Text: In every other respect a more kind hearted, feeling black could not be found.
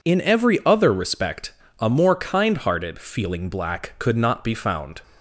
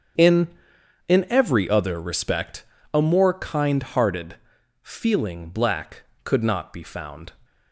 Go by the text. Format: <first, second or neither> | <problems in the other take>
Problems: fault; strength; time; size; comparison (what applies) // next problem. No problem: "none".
first | starts louder than the rest; strong; until 1.7 s; 7.5 dB // says "In" twice; at 1.0 s // pauses between "respect" and "a"; slight; at 2.6 s; 0.28 s long; slight in the first